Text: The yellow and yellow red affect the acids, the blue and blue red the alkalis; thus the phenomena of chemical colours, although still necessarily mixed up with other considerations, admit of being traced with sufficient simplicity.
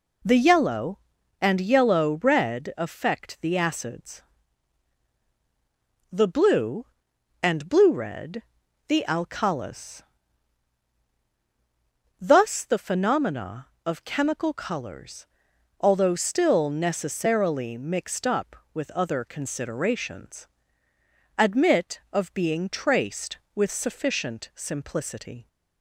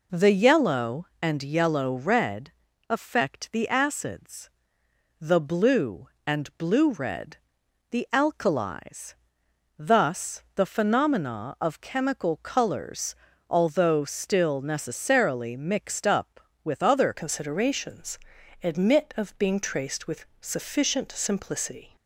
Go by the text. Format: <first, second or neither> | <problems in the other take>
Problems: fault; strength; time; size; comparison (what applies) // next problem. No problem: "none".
first | pauses between "red" and "affect"; at 2.4 s; 0.38 s long // pauses between "red" and "the"; noticeable; at 7.3 s; 0.56 s long; also in the first // changes voice at "considerations"; from 17.1 s on; 4.8 s long // pauses between "with" and "sufficient"; slight; at 20.2 s; 0.16 s long